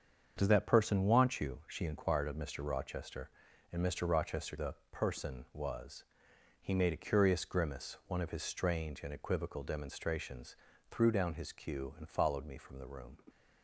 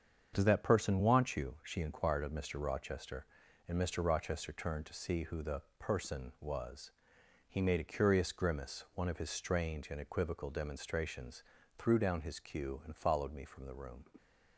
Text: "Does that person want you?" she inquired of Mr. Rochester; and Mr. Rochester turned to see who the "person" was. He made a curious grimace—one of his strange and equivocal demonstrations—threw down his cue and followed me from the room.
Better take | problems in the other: second | starts louder than the rest; until 1.4 s; 7 dB; strong in the second // skips "turned to see who"; at 4.5 s // pauses between "the" and "person"; slight; at 4.7 s; 0.16 s long; slight in the second

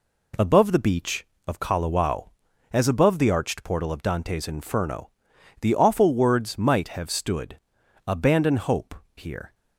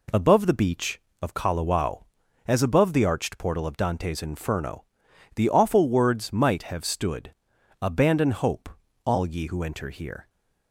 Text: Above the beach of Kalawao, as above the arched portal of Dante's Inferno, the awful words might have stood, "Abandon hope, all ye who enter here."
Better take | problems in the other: second | skips "all ye who enter"; at 9.0 s

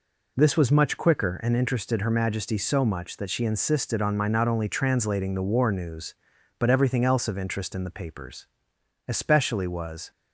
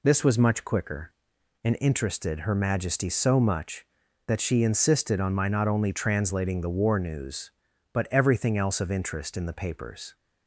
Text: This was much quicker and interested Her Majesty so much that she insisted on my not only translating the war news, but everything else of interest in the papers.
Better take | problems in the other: second | goes on to say "Especially was"; noticeable; from 9.0 s on; 1.0 s long

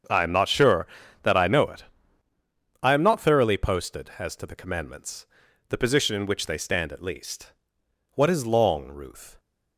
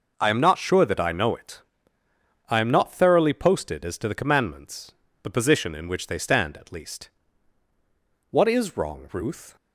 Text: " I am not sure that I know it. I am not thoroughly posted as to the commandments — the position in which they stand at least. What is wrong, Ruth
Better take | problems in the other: second | starts louder than the rest; until 1.4 s; 7 dB // says "long" for "wrong"; at 8.4 s

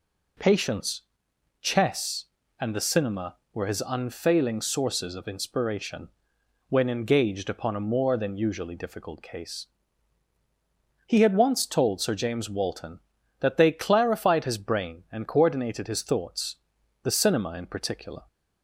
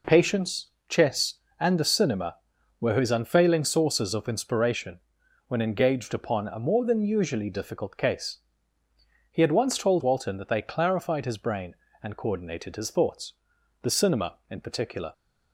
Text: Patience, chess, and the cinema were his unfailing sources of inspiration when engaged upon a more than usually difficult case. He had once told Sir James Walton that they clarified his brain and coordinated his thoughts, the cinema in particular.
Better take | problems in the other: first | pauses between "inspiration" and "when"; noticeable; at 4.9 s; 0.48 s long; noticeable in the first // skips "Sir James"; at 10.0 s

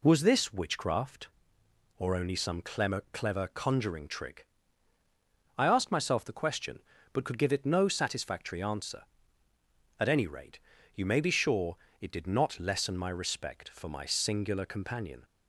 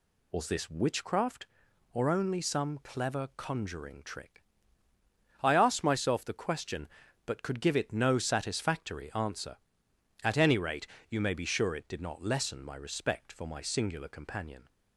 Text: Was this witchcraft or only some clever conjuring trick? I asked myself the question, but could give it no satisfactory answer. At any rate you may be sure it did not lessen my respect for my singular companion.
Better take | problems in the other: second | says "clever" twice; at 3.1 s // pauses between "rate" and "you"; slight; at 10.5 s; 0.34 s long; slight in the second // pauses between "sure" and "it"; slight; at 11.7 s; 0.24 s long

